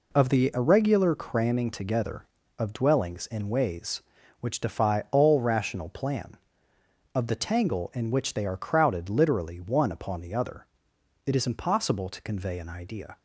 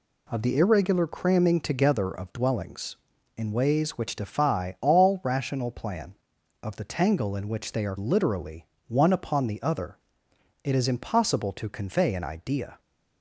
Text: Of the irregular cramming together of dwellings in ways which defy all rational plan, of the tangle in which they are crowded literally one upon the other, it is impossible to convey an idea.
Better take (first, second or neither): first